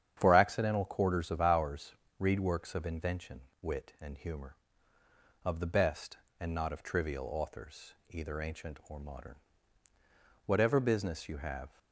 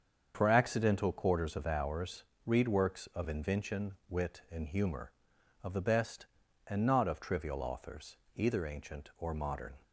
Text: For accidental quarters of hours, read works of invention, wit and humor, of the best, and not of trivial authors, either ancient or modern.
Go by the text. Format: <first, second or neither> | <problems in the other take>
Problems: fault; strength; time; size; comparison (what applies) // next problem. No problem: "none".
second | starts louder than the rest; strong; until 1.1 s; 9 dB; also in the second // goes on to say "Whatever business you have"; noticeable; from 10.4 s on; 1.2 s long